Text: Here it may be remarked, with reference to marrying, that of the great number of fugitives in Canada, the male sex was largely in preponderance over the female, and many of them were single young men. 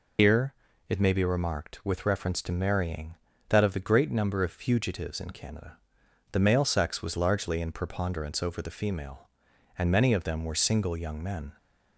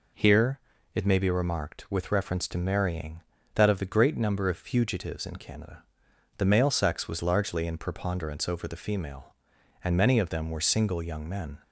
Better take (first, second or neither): second